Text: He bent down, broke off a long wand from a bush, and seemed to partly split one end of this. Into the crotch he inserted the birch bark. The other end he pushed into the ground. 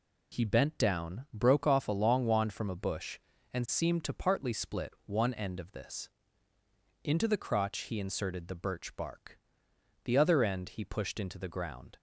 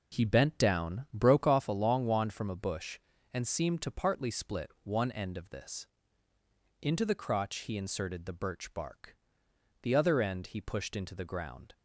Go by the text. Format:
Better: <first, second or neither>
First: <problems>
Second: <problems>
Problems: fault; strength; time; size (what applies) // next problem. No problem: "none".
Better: first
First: none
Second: starts louder than the rest; noticeable; until 1.7 s; 4 dB